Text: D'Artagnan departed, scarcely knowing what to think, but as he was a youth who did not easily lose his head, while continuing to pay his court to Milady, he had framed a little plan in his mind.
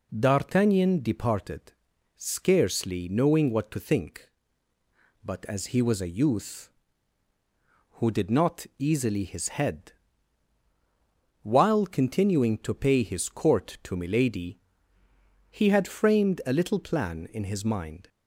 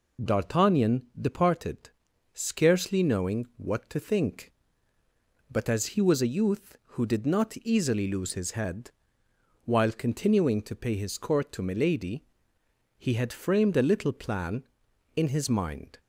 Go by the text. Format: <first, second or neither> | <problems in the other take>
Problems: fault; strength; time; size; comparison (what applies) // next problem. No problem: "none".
second | skips "lose"; at 9.2 s